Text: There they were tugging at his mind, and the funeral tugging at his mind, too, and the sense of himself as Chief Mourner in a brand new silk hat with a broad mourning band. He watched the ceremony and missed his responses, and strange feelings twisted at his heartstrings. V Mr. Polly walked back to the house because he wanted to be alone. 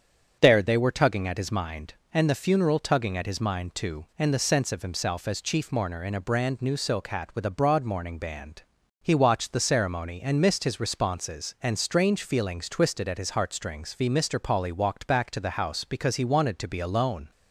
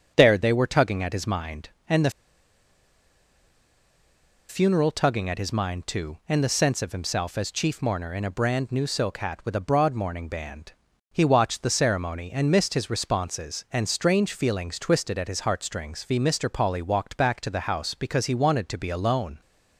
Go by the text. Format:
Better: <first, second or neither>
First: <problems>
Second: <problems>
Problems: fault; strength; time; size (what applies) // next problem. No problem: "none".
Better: first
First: starts louder than the rest; strong; until 1.4 s; 7.5 dB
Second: starts louder than the rest; strong; until 1.1 s; 7.5 dB // pauses between "the" and "funeral"; strong; at 2.0 s; 2.3 s long